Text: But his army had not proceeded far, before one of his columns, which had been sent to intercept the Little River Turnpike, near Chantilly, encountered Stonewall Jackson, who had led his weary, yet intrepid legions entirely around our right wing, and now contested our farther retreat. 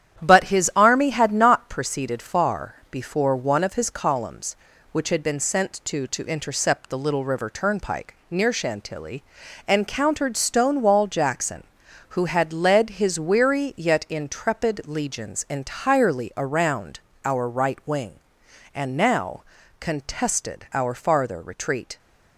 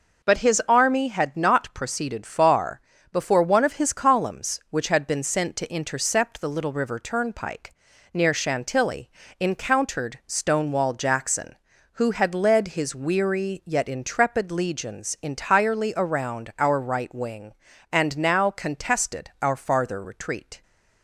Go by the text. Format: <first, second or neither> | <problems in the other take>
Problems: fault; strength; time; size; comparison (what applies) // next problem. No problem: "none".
second | starts louder than the rest; strong; until 1.2 s; 10 dB // says "to" twice; at 6.0 s // pauses between "around" and "our"; slight; at 17.0 s; 0.26 s long // pauses between "now" and "contested"; at 19.4 s; 0.38 s long